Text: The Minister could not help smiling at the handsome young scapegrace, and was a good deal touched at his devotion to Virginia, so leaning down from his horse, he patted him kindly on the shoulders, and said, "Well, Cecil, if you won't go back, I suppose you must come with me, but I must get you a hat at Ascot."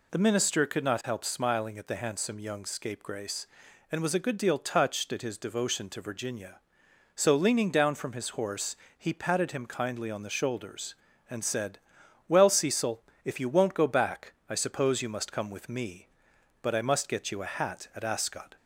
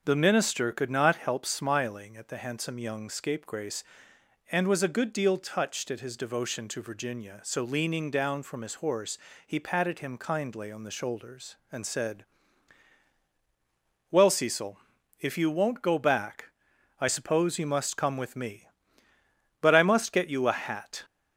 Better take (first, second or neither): first